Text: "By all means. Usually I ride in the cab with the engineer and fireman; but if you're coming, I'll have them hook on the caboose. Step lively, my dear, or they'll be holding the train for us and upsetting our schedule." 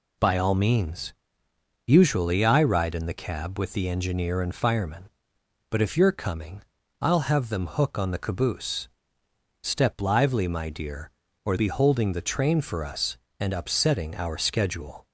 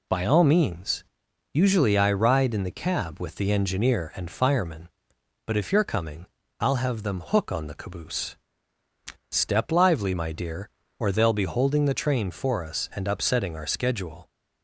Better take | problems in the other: second | skips "they'll"; at 11.5 s

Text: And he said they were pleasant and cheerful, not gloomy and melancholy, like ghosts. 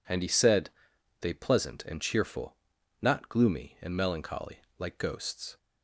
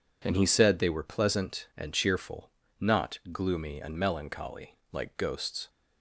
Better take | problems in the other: second | pauses between "said" and "they"; noticeable; at 0.6 s; 0.50 s long // skips "were"; at 1.3 s

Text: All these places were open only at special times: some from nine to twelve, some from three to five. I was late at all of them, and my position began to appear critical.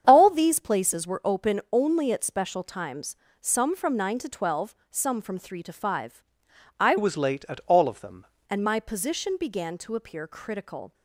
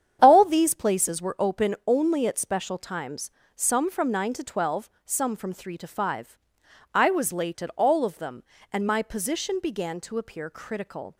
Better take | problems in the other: second | starts louder than the rest; strong; until 1.0 s; 8 dB; strong in the second // changes voice from "was" to "them"; from 6.9 to 8.2 s; 1.3 s long

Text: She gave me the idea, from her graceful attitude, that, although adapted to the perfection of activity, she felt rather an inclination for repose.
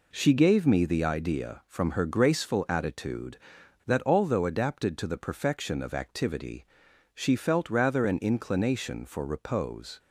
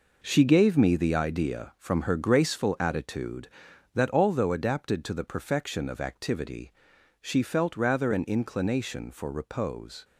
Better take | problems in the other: first | gets quieter; strong; throughout; 9.5 dB

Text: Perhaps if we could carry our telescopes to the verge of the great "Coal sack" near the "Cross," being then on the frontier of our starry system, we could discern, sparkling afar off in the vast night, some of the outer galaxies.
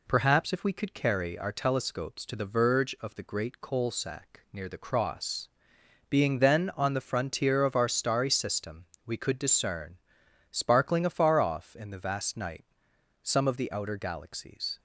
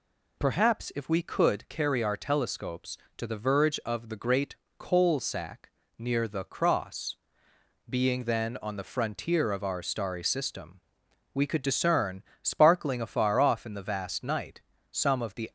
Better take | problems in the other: first | pauses between "great" and "Coal"; slight; at 4.5 s; 0.24 s long // pauses between "sack" and "near"; slight; at 5.6 s; 0.30 s long // stops before "outer galaxies"; at 15.4 s

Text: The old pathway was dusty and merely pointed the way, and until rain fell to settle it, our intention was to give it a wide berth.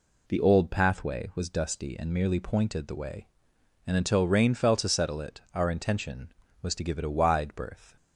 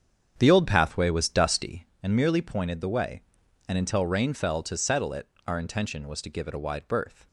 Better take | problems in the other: first | starts louder than the rest; strong; until 2.0 s; 7.5 dB

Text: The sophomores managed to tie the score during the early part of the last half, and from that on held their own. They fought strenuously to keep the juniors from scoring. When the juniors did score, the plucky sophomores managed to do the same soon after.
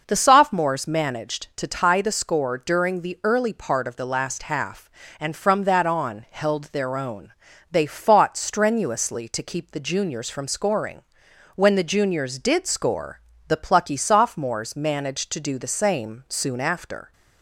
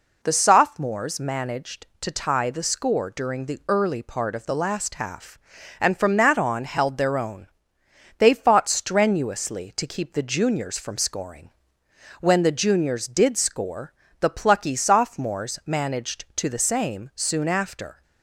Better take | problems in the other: first | skips "do"; at 16.4 s

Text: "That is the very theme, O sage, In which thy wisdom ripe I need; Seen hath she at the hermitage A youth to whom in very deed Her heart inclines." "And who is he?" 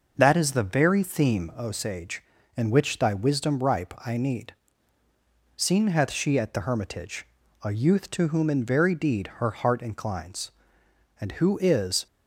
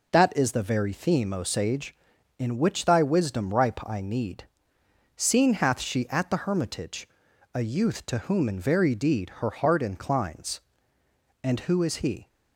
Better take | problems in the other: second | pauses between "hermitage" and "A"; slight; at 7.2 s; 0.36 s long; also in the second // stops before "he"; at 12.0 s

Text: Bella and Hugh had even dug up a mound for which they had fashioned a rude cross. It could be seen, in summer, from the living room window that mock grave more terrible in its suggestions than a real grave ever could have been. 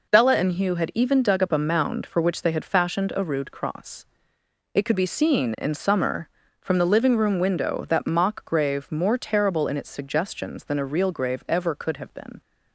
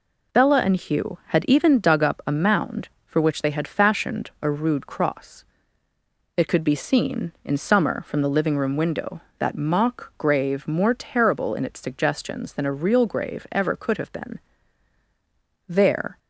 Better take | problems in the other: first | goes on to say "There"; from 15.6 s on; 0.50 s long

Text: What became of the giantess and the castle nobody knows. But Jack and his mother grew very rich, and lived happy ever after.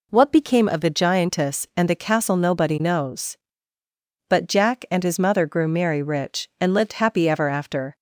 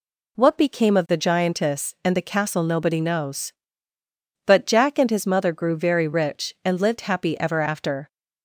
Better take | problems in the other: second | says "merry" for "very"; at 5.6 s

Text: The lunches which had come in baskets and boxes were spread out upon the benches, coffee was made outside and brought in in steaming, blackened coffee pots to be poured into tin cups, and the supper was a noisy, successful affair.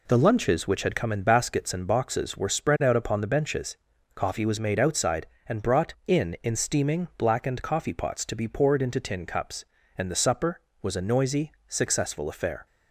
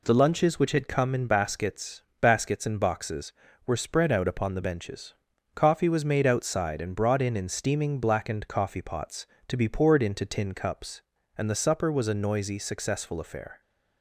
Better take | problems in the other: first | says "baskets" twice; at 2.1 s

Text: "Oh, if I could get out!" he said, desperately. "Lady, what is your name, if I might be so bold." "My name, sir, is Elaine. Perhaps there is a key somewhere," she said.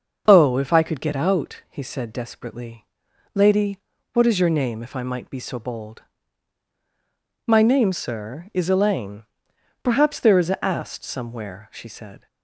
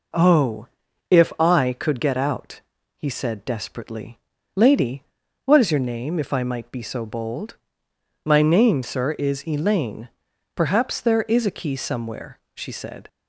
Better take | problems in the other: second | starts louder than the rest; noticeable; until 1.2 s; 6 dB // says "ast" for "key"; at 10.6 s

